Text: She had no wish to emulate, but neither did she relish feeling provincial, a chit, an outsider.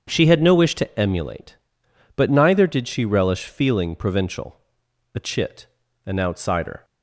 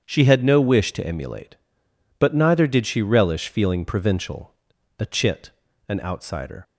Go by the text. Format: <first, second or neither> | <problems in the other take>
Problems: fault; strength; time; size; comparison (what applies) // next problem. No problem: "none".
neither | starts louder than the rest; strong; the same in both